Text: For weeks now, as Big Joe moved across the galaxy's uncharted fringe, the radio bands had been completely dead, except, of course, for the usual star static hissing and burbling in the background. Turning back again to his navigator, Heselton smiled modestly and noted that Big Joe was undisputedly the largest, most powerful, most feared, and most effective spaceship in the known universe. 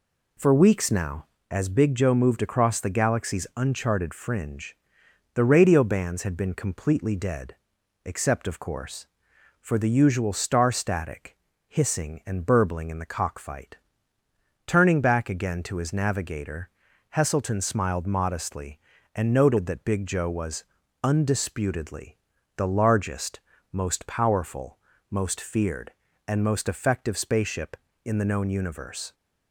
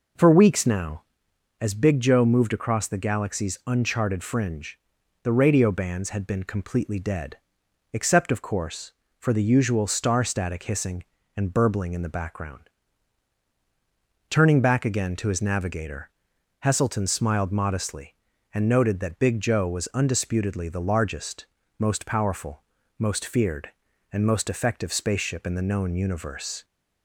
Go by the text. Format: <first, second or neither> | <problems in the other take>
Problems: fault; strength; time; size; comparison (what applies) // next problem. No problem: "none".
second | pauses between "static" and "hissing"; slight; at 11.3 s; 0.30 s long // says "cockfight" for "background"; at 13.1 s // pauses between "was" and "undisputedly"; at 20.6 s; 0.40 s long // pauses between "undisputedly" and "the"; at 22.1 s; 0.40 s long